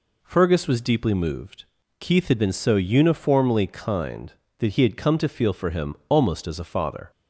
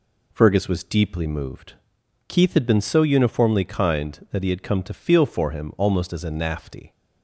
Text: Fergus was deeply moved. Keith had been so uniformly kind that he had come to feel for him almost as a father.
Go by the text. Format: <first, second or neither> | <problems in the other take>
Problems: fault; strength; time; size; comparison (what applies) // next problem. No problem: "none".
first | says "nafty" for "father"; at 6.2 s